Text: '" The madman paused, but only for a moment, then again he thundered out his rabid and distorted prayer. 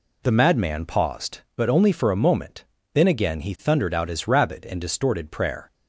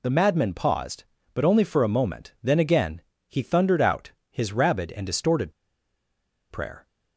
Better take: first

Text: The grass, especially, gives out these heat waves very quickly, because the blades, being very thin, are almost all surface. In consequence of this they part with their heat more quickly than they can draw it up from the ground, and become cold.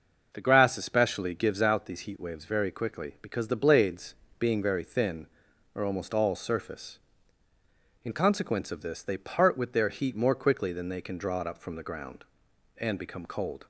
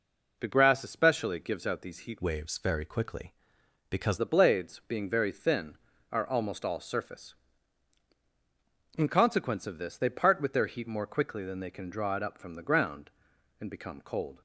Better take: first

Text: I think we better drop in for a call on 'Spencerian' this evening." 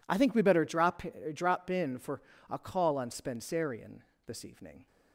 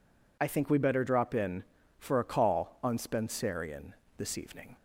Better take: second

